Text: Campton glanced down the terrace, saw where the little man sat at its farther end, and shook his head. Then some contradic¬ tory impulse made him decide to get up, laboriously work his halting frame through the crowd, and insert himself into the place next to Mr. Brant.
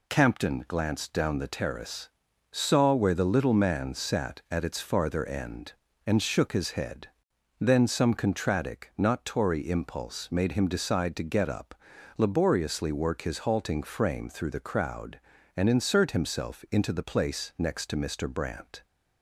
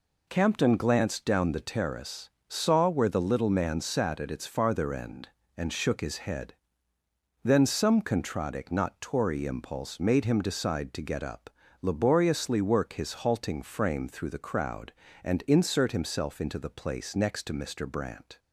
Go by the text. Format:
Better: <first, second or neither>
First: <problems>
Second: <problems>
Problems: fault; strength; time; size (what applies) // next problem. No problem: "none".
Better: neither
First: none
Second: none